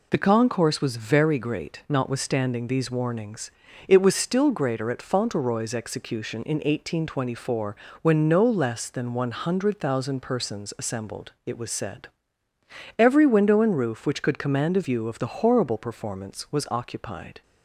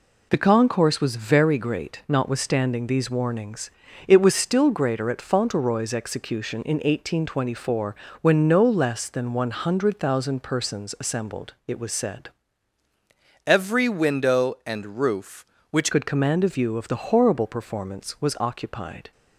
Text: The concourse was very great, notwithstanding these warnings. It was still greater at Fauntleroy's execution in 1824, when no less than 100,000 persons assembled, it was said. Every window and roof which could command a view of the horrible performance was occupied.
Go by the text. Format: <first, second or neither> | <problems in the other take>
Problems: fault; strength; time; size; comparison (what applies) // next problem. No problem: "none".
first | changes voice from "Every" to "which"; from 13.4 to 15.9 s; 2.5 s long